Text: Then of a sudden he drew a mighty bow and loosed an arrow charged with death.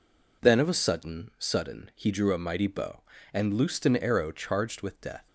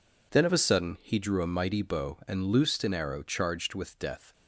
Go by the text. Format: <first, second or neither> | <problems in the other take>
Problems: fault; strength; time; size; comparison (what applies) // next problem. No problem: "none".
second | says "sudden" twice; at 1.3 s